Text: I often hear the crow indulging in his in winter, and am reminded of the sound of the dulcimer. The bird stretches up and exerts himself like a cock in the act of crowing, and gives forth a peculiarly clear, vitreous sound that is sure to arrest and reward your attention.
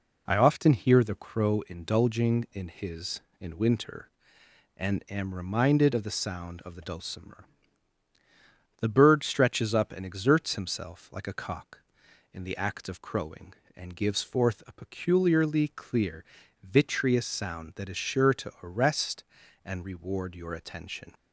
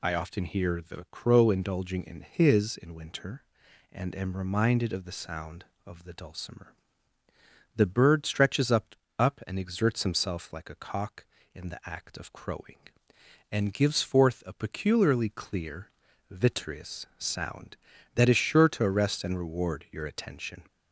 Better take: first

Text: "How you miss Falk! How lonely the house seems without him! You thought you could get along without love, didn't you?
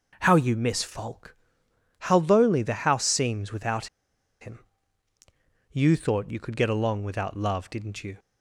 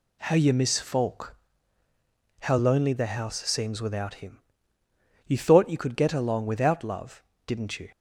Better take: second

